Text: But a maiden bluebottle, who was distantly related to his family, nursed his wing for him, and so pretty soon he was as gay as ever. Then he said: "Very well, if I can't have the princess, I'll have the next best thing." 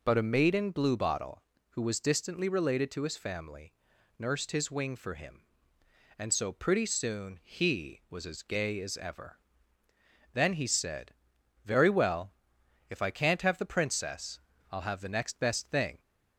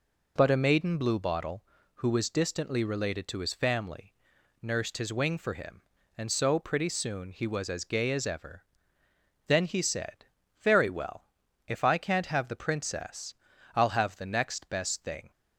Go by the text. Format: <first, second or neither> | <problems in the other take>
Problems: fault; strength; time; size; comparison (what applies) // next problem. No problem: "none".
neither | none